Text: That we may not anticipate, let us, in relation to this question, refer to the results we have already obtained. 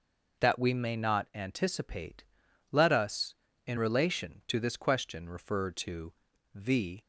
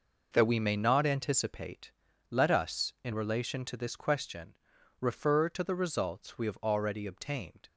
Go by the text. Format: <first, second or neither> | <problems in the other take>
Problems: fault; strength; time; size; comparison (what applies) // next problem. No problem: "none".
second | pauses between "to" and "the"; at 6.1 s; 0.42 s long // stops before "results we have already obtained"; at 7.0 s